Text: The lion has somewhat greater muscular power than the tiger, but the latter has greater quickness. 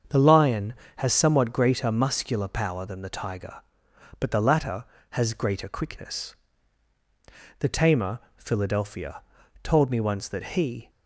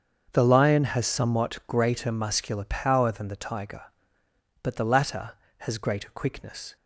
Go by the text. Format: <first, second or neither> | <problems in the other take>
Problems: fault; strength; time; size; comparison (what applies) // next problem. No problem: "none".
second | starts louder than the rest; until 1.3 s; 7 dB; also in the second // goes on to say "The tamer Philadelphia told me once that he"; strong; from 7.5 s on; 3.3 s long